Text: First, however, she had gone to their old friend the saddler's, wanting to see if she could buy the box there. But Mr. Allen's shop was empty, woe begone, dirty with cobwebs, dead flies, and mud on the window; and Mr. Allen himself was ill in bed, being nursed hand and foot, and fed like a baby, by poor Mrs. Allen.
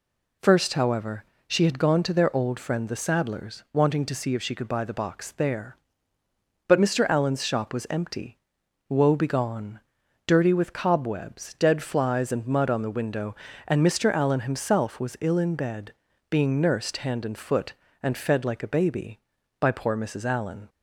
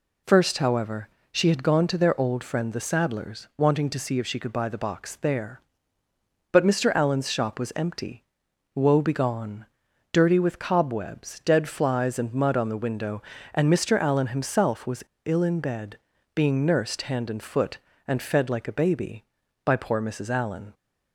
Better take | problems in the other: first | pauses between "was" and "ill"; slight; at 15.0 s; 0.22 s long

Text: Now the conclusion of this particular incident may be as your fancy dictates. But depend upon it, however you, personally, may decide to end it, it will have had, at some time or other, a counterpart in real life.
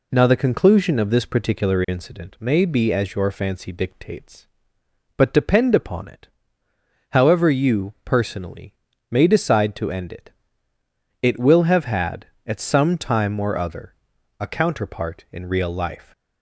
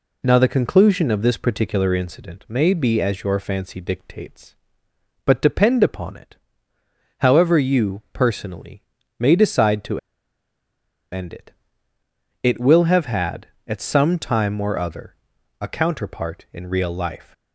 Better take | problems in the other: first | pauses between "to" and "end"; at 9.9 s; 1.1 s long

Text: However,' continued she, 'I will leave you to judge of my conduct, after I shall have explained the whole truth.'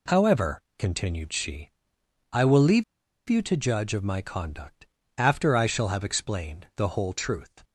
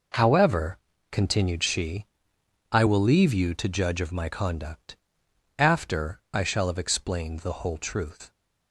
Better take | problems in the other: second | pauses between "leave" and "you"; noticeable; at 2.8 s; 0.45 s long

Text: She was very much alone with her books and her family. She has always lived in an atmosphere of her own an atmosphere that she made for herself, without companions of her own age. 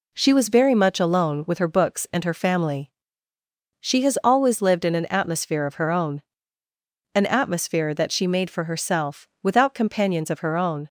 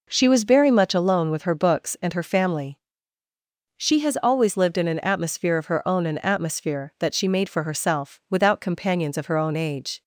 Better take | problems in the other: second | pauses between "own" and "an"; noticeable; at 6.2 s; 0.94 s long // stops before "age"; at 10.8 s

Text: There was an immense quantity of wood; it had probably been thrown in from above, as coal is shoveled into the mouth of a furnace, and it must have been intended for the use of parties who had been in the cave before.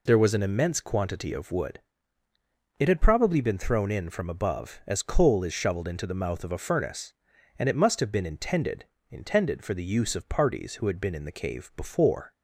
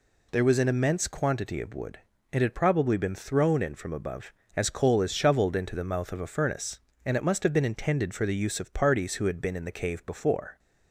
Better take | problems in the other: second | says "intended" twice; at 9.1 s

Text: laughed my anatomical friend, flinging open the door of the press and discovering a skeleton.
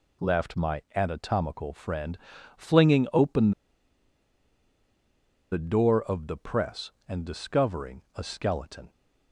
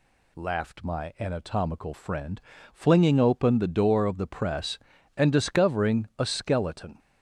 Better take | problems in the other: second | pauses between "open" and "the"; strong; at 3.5 s; 2.0 s long

